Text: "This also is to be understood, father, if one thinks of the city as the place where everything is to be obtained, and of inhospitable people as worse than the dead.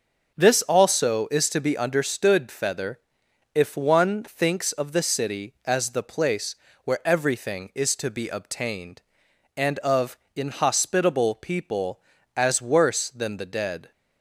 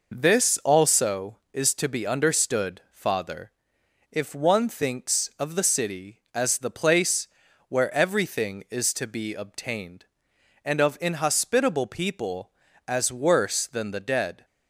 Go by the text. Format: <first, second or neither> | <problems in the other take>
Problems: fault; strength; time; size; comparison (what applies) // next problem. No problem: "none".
second | says "feather" for "father"; at 2.4 s // pauses between "place" and "where"; slight; at 6.5 s; 0.30 s long; also in the second // pauses between "of" and "inhospitable"; slight; at 10.1 s; 0.18 s long